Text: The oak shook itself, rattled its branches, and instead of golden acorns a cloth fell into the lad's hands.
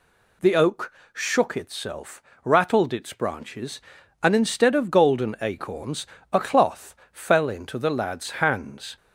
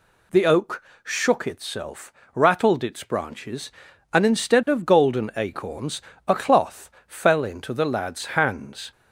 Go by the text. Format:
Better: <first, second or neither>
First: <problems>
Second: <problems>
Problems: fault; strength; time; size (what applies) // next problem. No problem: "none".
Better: neither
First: pauses between "oak" and "shook"; slight; at 0.9 s; 0.22 s long // pauses between "acorns" and "a"; slight; at 6.0 s; 0.24 s long // pauses between "cloth" and "fell"; slight; at 6.9 s; 0.16 s long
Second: pauses between "oak" and "shook"; slight; at 0.8 s; 0.22 s long // pauses between "acorns" and "a"; slight; at 6.0 s; 0.24 s long // pauses between "cloth" and "fell"; slight; at 6.9 s; 0.16 s long